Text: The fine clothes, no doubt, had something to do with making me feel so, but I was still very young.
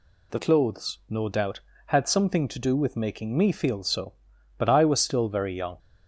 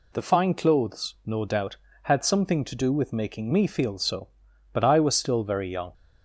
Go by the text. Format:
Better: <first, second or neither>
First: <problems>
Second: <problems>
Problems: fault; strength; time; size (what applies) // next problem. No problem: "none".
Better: second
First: skips "fine"; at 0.3 s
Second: none